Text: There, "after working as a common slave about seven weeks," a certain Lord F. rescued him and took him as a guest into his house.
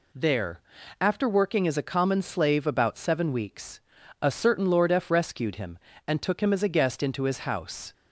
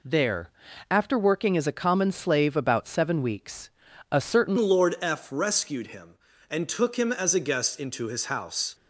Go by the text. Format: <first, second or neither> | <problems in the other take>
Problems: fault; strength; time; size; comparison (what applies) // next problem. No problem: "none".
first | changes voice at "Lord"; from 4.5 s on; 4.2 s long